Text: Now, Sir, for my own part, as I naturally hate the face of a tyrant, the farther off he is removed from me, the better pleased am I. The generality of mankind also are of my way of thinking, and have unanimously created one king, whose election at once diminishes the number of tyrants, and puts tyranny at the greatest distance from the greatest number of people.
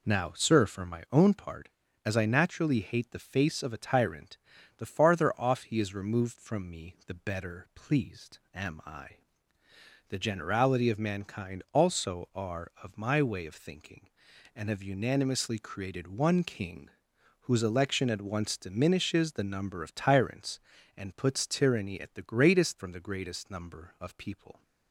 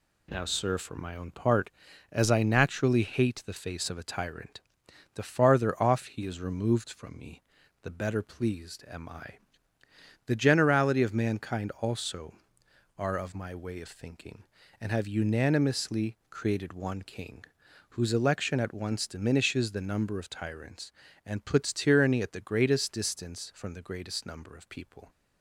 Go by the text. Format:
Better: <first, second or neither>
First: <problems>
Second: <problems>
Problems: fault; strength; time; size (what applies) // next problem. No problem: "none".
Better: second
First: skips "distance"; at 22.7 s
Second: none